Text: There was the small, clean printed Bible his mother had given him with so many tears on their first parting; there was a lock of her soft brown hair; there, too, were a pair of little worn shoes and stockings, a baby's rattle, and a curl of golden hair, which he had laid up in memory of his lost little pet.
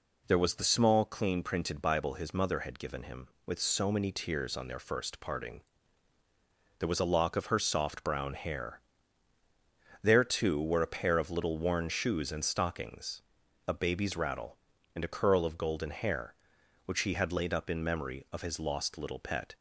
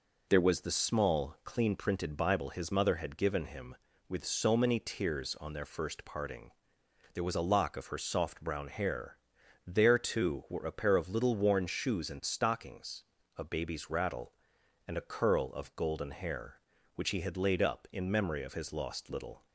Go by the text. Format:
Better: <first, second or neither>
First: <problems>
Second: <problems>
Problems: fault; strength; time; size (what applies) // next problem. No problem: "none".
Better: first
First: none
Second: stops before "pet"; at 19.4 s